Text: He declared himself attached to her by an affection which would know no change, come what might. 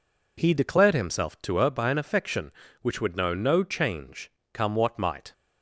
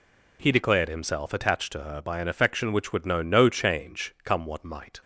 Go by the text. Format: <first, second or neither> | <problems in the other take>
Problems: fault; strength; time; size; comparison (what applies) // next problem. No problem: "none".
second | skips "attached"; at 1.4 s